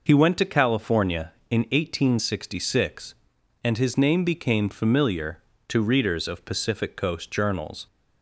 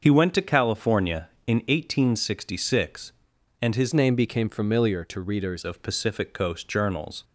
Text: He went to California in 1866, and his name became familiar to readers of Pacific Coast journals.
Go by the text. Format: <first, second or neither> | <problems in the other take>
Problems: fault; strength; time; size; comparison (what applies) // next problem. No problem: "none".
first | starts louder than the rest; until 1.0 s; 6.5 dB // changes voice from "name" to "readers"; from 3.9 to 5.6 s; 1.7 s long